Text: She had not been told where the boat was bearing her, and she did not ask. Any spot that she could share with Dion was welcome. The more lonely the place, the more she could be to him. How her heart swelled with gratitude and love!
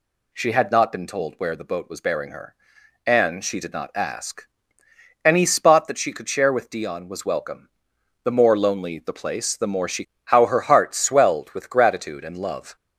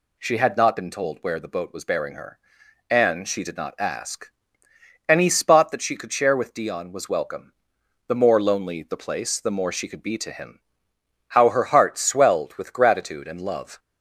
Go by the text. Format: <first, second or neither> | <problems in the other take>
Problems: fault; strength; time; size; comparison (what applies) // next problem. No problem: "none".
second | skips "could be to him"; at 10.1 s